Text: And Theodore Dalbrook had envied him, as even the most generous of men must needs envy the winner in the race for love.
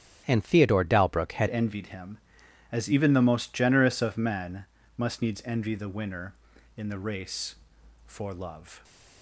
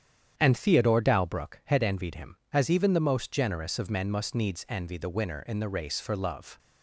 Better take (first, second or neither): second